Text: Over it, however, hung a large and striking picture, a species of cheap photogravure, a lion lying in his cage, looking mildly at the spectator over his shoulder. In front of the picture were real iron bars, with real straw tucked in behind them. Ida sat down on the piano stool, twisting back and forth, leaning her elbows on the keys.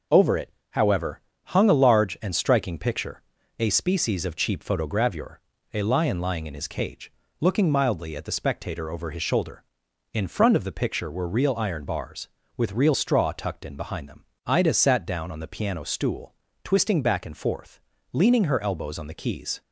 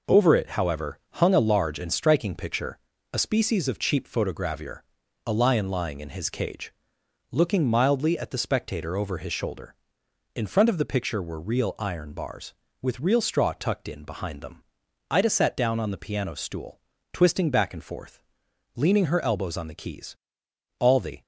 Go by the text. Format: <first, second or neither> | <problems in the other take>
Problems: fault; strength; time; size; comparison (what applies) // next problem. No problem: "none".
first | goes on to say "All the"; slight; from 20.8 s on; 0.42 s long